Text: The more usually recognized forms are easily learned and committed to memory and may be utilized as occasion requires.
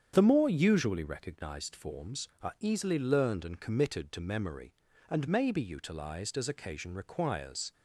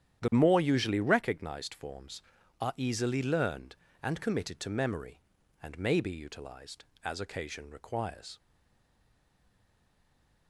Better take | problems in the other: first | starts louder than the rest; strong; until 1.2 s; 10 dB; strong in the first // stays silent after the last word; from 8.3 s on; 2.1 s long

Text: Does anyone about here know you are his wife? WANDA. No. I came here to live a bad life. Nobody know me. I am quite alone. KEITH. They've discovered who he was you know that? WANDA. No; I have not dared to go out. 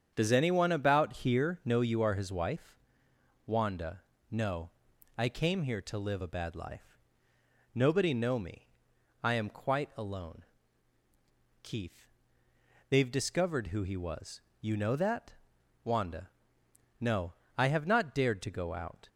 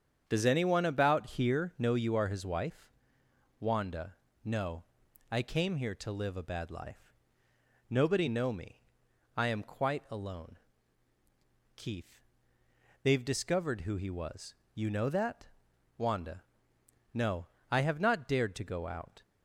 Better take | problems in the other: neither | starts louder than the rest; strong; the same in both // pauses between "was" and "you"; slight; the same in both

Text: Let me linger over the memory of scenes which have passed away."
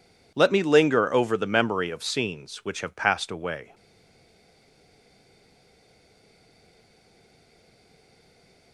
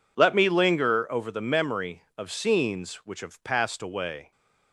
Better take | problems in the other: second | stays silent after the last word; strong; from 3.7 s on; 5.0 s long

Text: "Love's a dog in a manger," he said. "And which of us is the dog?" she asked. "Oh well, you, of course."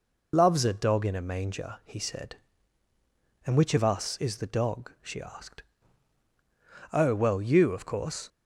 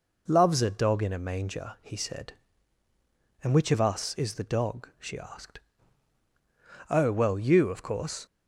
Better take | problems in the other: second | loses the start of "Love's"; at 0.3 s; 30 ms

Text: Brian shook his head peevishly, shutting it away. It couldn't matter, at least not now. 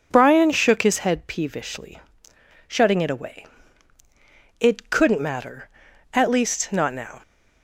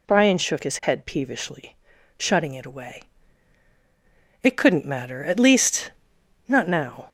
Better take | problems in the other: first | gets louder; slight; throughout; 3 dB // pauses between "least" and "not"; noticeable; at 5.9 s; 0.56 s long

